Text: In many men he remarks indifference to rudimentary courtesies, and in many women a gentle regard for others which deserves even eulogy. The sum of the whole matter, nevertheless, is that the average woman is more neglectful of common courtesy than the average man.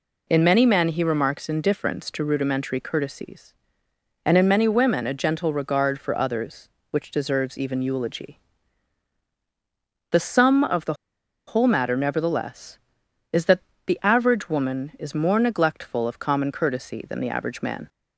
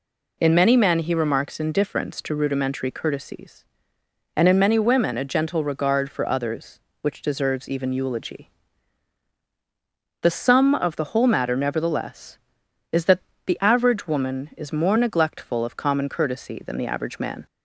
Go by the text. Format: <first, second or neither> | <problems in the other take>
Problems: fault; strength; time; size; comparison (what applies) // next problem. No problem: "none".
second | pauses between "the" and "whole"; noticeable; at 10.9 s; 0.52 s long // pauses between "that" and "the"; slight; at 13.6 s; 0.26 s long; slight in the second